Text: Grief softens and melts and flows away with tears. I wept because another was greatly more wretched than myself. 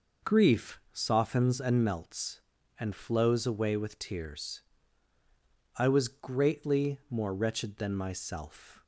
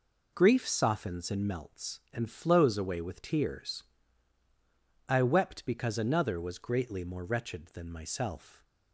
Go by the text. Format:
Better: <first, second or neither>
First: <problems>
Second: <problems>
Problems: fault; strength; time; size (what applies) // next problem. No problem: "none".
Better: second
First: skips "wept because another"; at 5.8 s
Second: none